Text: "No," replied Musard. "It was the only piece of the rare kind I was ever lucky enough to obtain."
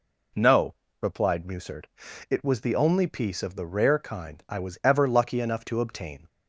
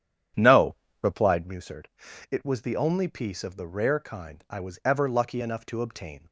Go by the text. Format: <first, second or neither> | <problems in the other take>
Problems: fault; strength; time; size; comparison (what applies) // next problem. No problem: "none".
first | starts louder than the rest; strong; until 1.5 s; 9.5 dB